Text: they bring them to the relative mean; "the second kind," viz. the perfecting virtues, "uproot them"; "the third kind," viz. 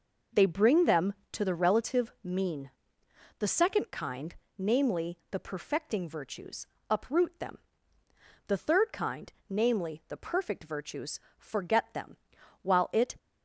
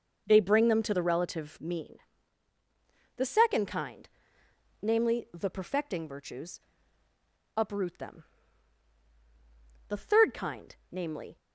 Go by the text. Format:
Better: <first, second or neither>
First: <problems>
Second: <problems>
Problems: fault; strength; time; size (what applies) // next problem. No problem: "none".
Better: second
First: goes on to say "the perfect virtues forget them while it"; strong; from 10.0 s on; 3.0 s long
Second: none